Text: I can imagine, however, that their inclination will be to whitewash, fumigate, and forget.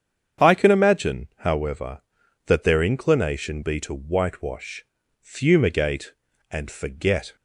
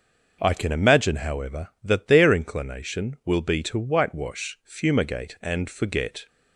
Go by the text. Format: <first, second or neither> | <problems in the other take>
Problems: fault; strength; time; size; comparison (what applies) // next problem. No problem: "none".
second | starts louder than the rest; strong; until 1.5 s; 8 dB; also in the second // skips "will"; at 3.6 s